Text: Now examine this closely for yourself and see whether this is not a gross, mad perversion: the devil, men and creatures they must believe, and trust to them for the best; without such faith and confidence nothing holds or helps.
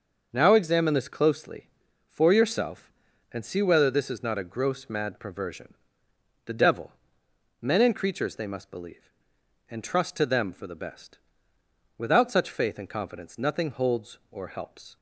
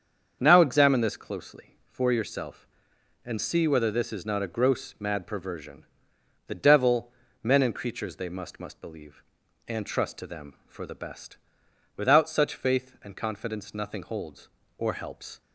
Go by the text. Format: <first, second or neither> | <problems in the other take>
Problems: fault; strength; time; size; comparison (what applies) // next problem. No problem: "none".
first | starts louder than the rest; strong; until 1.4 s; 7 dB; also in the first // says "must" twice; at 8.5 s